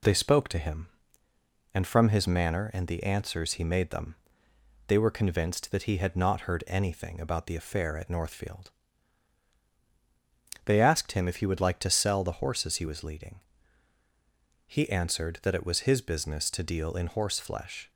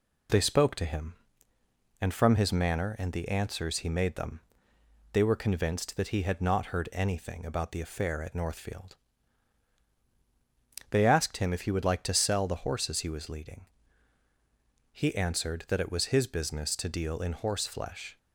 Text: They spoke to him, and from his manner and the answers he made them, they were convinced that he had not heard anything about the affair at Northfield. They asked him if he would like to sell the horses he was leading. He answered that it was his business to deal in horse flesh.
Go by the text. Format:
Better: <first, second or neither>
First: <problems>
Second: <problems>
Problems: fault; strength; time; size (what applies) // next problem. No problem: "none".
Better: neither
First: none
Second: none